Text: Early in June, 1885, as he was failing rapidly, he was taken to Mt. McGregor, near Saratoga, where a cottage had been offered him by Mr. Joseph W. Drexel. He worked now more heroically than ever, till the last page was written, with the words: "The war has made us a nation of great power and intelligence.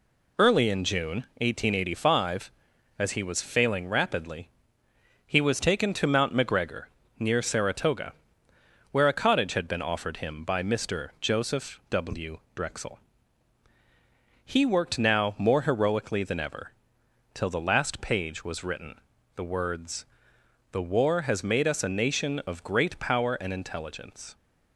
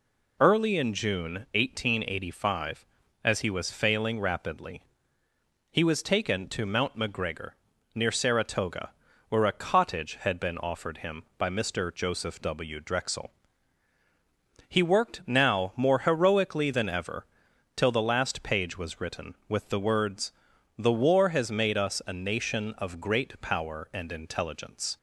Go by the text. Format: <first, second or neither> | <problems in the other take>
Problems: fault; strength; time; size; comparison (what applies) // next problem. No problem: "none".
second | skips "with"; at 19.1 s